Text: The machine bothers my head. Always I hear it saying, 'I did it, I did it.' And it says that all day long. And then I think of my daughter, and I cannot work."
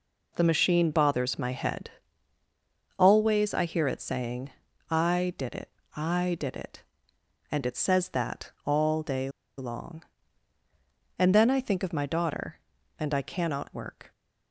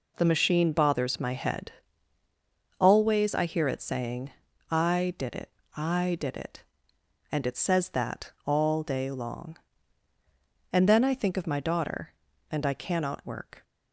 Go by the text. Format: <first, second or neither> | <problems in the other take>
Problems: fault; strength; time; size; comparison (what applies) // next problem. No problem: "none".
second | pauses between "day" and "long"; slight; at 9.2 s; 0.29 s long